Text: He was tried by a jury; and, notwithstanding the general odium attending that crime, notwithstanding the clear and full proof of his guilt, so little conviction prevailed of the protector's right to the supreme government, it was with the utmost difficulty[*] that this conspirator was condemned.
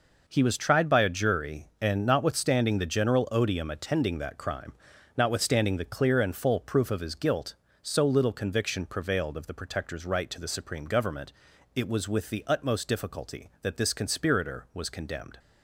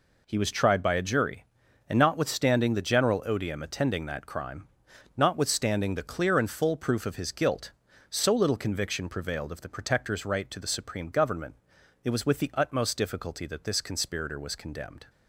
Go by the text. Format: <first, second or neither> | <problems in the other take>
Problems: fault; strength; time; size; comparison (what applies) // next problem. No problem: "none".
neither | none